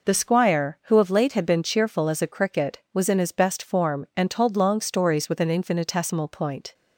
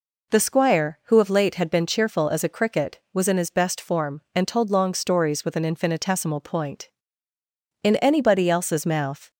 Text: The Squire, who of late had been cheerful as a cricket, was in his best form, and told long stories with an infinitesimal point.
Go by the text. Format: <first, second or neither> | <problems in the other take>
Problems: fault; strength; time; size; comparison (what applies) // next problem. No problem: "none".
first | goes on to say "In anybody else's mouth"; from 7.8 s on; 1.4 s long